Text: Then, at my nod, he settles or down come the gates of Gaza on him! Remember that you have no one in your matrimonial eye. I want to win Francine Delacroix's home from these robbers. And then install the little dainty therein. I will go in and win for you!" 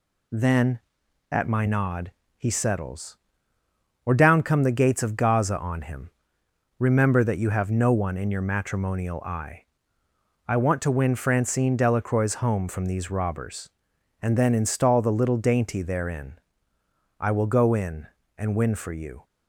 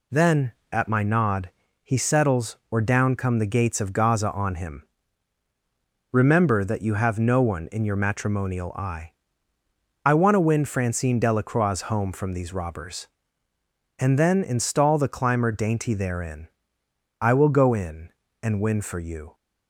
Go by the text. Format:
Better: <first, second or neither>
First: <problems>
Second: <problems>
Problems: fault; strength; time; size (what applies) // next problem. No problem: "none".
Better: first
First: none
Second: says "climber" for "little"; at 15.0 s